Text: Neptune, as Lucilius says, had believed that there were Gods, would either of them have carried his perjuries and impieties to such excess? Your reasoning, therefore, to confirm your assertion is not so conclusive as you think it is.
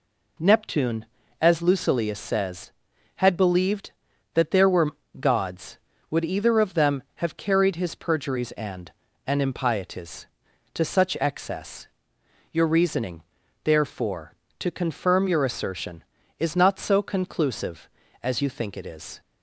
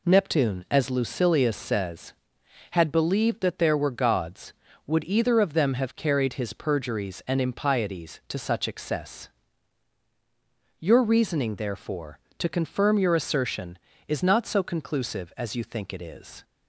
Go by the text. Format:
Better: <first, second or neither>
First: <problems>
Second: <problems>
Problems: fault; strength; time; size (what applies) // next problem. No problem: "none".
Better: second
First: pauses between "were" and "Gods"; slight; at 4.9 s; 0.26 s long // says "and" twice; at 9.2 s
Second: none